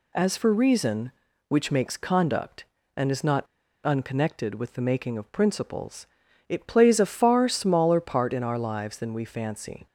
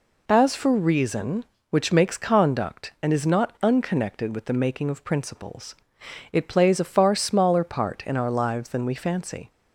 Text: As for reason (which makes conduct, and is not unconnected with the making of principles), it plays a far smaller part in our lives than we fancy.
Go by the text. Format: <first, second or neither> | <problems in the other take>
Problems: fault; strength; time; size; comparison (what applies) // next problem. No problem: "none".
second | pauses between "not" and "unconnected"; at 3.4 s; 0.39 s long